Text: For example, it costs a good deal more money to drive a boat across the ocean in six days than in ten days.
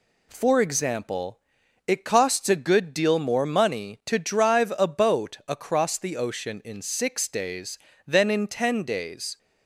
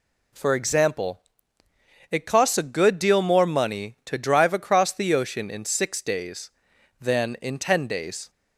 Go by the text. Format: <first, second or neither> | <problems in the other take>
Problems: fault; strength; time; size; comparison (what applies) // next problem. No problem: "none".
first | skips "a boat"; at 4.5 s